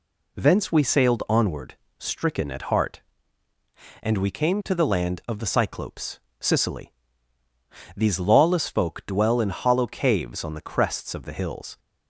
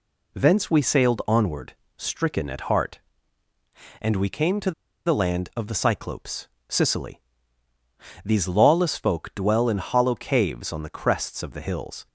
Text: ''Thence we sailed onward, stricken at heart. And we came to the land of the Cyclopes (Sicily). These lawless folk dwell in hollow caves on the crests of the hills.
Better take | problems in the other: first | pauses between "to" and "the"; slight; at 4.7 s; 0.35 s long

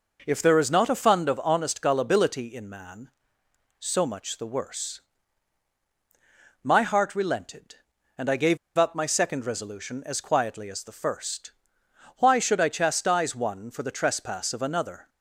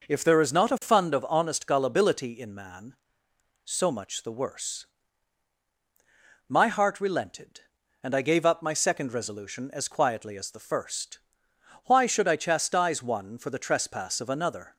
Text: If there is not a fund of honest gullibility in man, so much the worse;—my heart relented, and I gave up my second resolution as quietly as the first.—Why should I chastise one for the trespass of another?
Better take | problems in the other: second | pauses between "gave" and "up"; slight; at 8.5 s; 0.21 s long

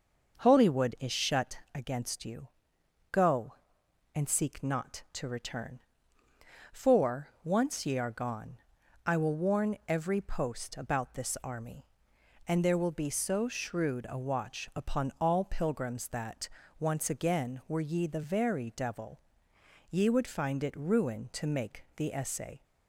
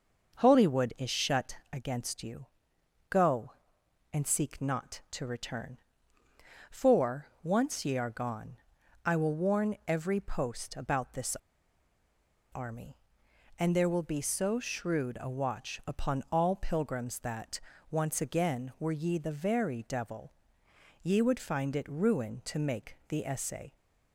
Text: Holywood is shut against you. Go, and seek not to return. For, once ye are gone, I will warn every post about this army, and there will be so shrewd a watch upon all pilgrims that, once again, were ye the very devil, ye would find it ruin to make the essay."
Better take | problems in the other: first | starts louder than the rest; until 1.4 s; 6 dB; also in the first // pauses between "this" and "army"; at 11.3 s; 1.1 s long

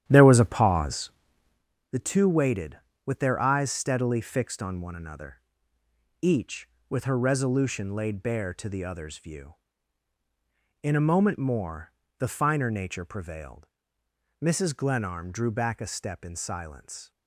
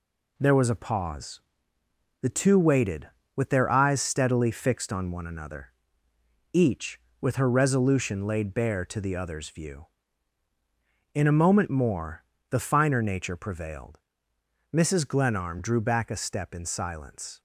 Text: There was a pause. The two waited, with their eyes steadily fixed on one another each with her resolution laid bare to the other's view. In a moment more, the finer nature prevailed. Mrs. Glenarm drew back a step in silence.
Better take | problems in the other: second | starts louder than the rest; strong; until 1.6 s; 11 dB // pauses between "another" and "each"; noticeable; at 5.4 s; 0.80 s long; noticeable in the second

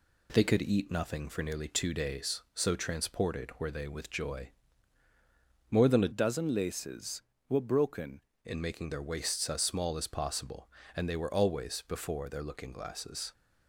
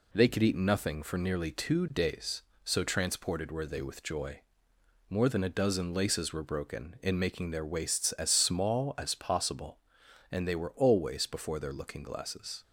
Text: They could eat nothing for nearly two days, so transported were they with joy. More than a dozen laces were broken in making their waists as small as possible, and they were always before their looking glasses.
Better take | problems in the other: second | changes voice from "dozen" to "broken"; from 6.1 to 8.2 s; 2.1 s long

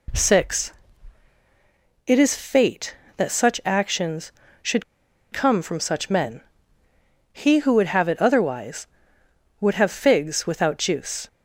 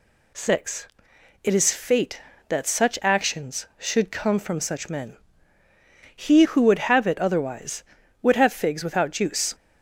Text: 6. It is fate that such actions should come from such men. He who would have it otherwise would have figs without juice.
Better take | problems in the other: second | pauses between "should" and "come"; noticeable; at 4.8 s; 0.48 s long

